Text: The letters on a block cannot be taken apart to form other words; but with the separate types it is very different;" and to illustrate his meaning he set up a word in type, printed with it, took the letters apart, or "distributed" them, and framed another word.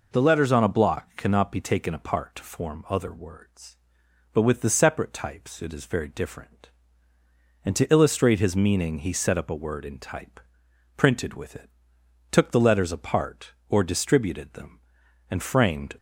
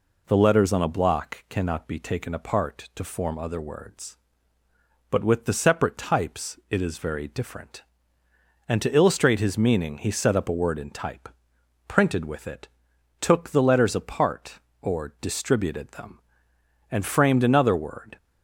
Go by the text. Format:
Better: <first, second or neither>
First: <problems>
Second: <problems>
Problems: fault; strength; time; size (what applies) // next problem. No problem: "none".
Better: second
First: stops before "another word"; at 15.9 s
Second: none